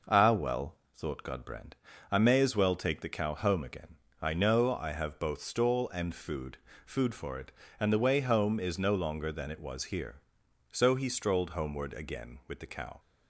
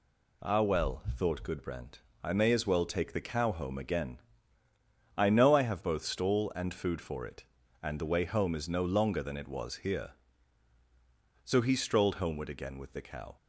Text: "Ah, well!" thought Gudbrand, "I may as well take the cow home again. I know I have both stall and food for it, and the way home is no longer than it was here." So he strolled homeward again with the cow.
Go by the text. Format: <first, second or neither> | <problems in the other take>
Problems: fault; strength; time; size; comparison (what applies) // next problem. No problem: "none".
second | says "food" twice; at 6.8 s